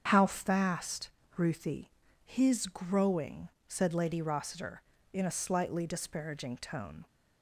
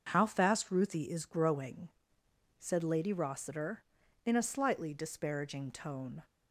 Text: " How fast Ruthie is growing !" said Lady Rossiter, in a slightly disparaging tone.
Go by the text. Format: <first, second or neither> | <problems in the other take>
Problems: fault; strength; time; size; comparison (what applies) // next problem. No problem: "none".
second | starts louder than the rest; strong; until 1.0 s; 7.5 dB; also in the second // pauses between "fast" and "Ruthie"; slight; at 1.1 s; 0.26 s long // says "his" for "is"; at 2.2 s